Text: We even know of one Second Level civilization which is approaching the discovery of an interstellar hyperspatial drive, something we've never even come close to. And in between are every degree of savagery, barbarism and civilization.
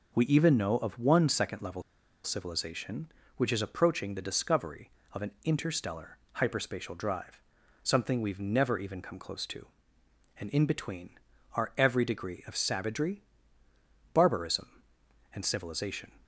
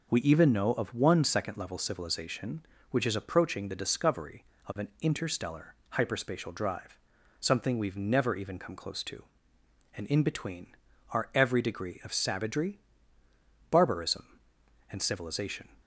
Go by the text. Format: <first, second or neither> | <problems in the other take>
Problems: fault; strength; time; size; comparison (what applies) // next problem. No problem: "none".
second | pauses between "Level" and "civilization"; at 1.8 s; 0.41 s long // pauses between "interstellar" and "hyperspatial"; slight; at 6.1 s; 0.18 s long; slight in the second